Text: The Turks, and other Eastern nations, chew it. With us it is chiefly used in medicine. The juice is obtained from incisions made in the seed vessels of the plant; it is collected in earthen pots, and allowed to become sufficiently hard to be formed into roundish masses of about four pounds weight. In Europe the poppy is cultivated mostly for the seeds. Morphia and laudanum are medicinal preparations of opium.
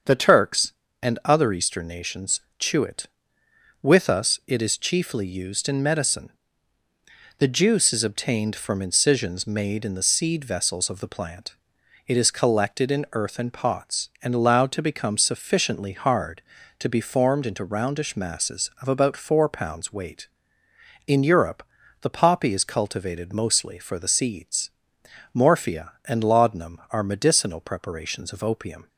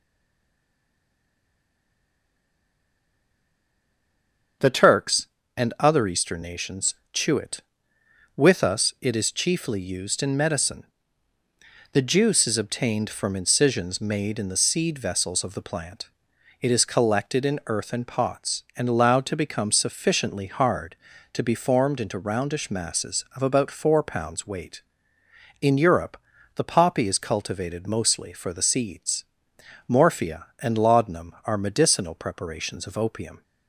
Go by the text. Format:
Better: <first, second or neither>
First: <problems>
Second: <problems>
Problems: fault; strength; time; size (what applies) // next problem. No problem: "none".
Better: first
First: starts louder than the rest; until 1.4 s; 7 dB // pauses between "Europe" and "the"; at 21.6 s; 0.38 s long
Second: stays silent before the first word; strong; until 4.6 s; 4.6 s long // starts louder than the rest; until 5.9 s; 7 dB // pauses between "Europe" and "the"; at 26.1 s; 0.38 s long